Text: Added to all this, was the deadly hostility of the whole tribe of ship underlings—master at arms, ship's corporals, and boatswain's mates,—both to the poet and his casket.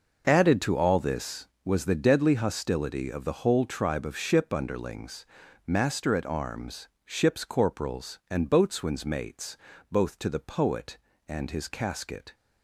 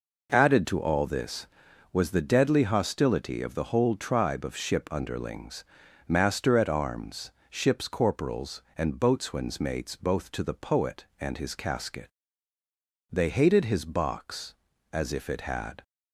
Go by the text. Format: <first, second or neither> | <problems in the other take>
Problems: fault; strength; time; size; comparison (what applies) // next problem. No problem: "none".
first | goes on to say "They hated his box as if it had"; strong; from 13.1 s on; 2.7 s long